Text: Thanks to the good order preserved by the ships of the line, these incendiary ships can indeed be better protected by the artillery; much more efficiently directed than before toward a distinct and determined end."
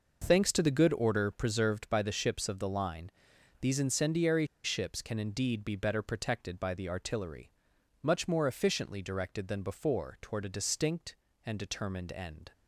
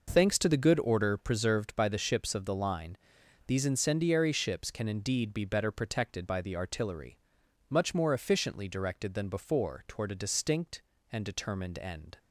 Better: second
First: pauses between "incendiary" and "ships"; slight; at 4.4 s; 0.17 s long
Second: none

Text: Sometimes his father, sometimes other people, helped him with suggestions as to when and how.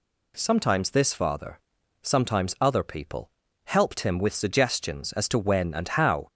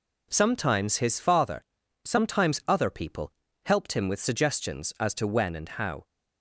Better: second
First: says "this" for "his"; at 0.8 s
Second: none

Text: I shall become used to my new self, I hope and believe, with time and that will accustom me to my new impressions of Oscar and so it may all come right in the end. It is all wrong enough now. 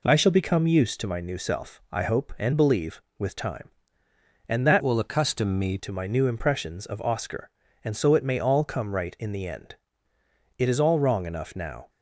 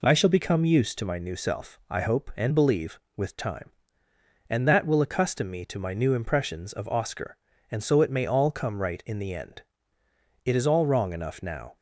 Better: second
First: changes voice from "will" to "me"; from 4.8 to 5.7 s; 0.9 s long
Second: none

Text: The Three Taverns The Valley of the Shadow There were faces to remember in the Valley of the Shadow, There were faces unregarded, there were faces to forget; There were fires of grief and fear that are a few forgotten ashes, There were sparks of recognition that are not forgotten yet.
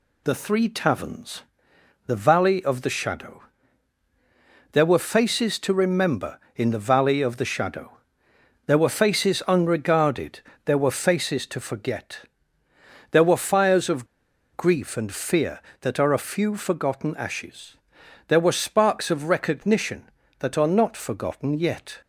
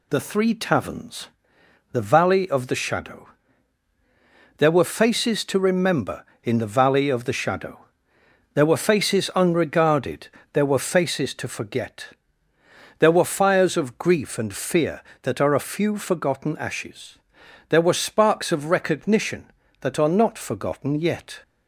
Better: second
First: pauses between "Taverns" and "The"; noticeable; at 1.4 s; 0.64 s long // pauses between "Shadow" and "There"; strong; at 3.4 s; 1.3 s long // pauses between "of" and "grief"; noticeable; at 14.0 s; 0.48 s long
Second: pauses between "Taverns" and "The"; noticeable; at 1.2 s; 0.64 s long // pauses between "Shadow" and "There"; strong; at 3.2 s; 1.3 s long

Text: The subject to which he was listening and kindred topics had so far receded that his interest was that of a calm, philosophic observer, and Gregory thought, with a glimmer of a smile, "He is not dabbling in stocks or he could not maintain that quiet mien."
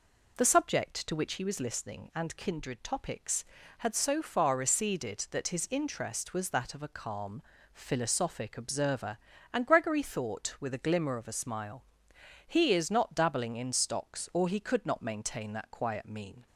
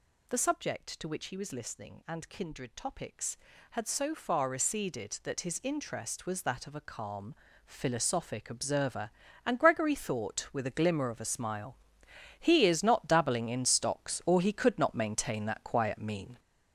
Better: first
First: none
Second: gets louder; strong; throughout; 7 dB

